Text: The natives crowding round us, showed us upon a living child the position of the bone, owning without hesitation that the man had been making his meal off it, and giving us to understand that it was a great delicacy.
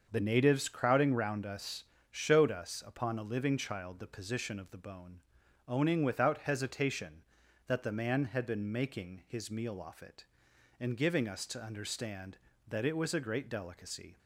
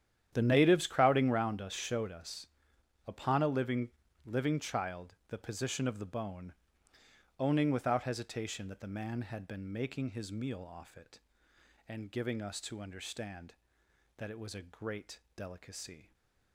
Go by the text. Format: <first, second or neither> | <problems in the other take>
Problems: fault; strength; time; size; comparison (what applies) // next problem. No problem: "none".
first | starts louder than the rest; strong; until 1.3 s; 10 dB; also in the first // pauses between "us" and "upon"; noticeable; at 2.4 s; 0.58 s long // says "living" twice; at 4.2 s // pauses between "great" and "delicacy"; slight; at 15.1 s; 0.16 s long